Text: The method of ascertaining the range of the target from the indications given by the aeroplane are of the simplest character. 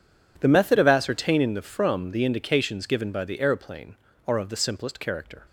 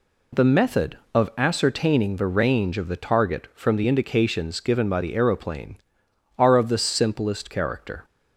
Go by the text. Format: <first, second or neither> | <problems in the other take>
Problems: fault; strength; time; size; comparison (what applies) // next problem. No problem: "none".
second | skips "range of the target"; at 1.6 s